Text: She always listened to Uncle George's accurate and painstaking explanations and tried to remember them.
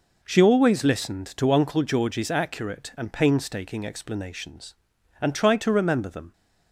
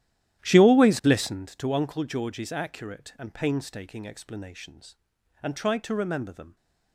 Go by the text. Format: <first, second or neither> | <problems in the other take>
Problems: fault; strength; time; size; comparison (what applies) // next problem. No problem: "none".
first | starts louder than the rest; strong; until 1.5 s; 12.5 dB